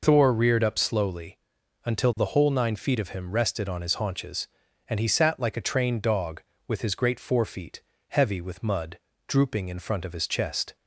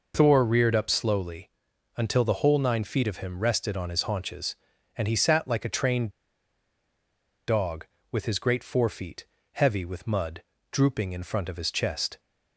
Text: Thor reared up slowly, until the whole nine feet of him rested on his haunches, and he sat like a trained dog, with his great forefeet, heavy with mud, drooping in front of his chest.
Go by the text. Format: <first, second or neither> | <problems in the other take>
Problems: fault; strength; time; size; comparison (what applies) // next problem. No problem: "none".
first | pauses between "trained" and "dog"; strong; at 6.0 s; 1.3 s long